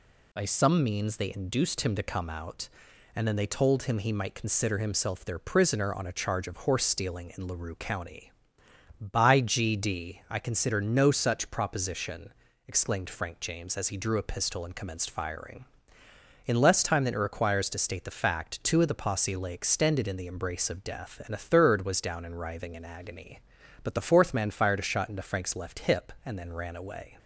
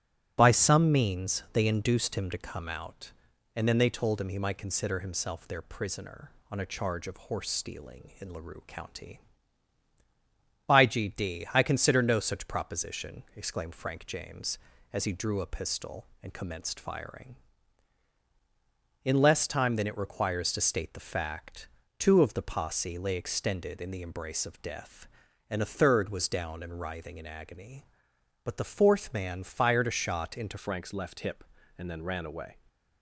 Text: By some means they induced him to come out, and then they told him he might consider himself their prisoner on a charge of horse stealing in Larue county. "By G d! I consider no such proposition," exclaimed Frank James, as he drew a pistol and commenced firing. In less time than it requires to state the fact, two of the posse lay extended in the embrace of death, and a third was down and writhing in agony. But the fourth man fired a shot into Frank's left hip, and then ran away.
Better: first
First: none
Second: starts louder than the rest; strong; until 1.4 s; 12.5 dB // changes voice at "Frank's"; from 30.5 s on; 2.0 s long

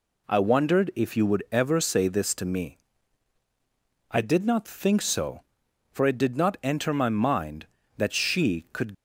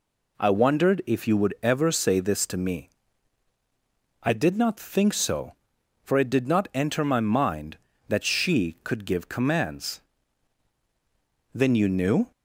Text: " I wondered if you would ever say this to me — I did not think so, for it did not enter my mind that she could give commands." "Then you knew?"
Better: second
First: stops before "give commands Then you knew"; at 8.9 s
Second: none

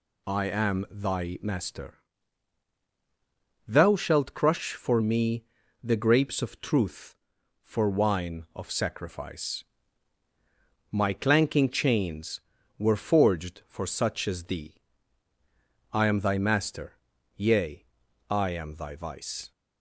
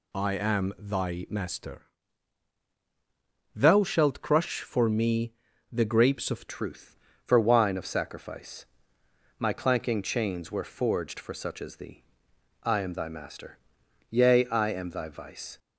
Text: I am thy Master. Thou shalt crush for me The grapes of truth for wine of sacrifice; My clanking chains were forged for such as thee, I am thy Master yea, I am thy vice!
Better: first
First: pauses between "me" and "The"; slight; at 5.4 s; 0.36 s long // pauses between "Master" and "yea"; at 16.9 s; 0.42 s long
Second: pauses between "me" and "The"; slight; at 5.3 s; 0.36 s long // changes voice at "truth"; from 6.4 s on; 9.1 s long // pauses between "Master" and "yea"; noticeable; at 13.5 s; 0.50 s long

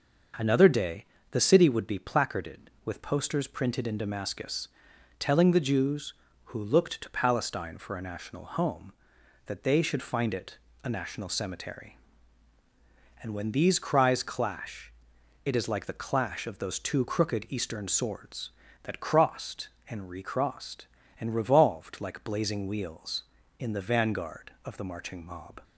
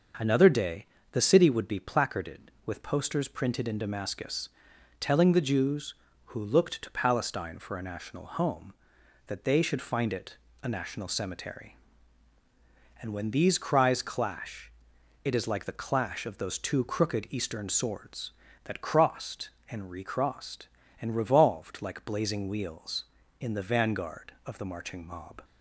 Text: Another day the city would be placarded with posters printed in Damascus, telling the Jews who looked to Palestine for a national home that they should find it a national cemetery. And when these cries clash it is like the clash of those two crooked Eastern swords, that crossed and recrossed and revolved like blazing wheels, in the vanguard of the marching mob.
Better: neither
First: starts louder than the rest; until 1.6 s; 6 dB // pauses between "day" and "the"; slight; at 1.0 s; 0.26 s long // pauses between "it" and "a"; slight; at 10.5 s; 0.26 s long // pauses between "clash" and "it"; noticeable; at 14.9 s; 0.54 s long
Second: starts louder than the rest; until 1.4 s; 6 dB // pauses between "day" and "the"; slight; at 0.8 s; 0.26 s long // pauses between "it" and "a"; slight; at 10.3 s; 0.26 s long // pauses between "clash" and "it"; noticeable; at 14.6 s; 0.54 s long

